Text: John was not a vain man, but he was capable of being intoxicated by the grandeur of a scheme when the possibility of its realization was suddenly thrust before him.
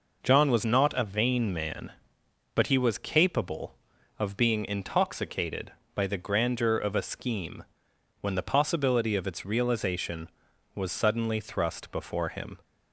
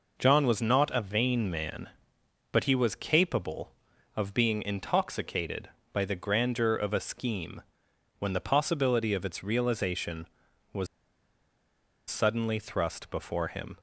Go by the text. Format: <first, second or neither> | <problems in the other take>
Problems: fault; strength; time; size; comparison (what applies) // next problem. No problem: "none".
first | pauses between "scheme" and "when"; noticeable; at 7.6 s; 0.58 s long; noticeable in the first // pauses between "was" and "suddenly"; at 10.8 s; 1.2 s long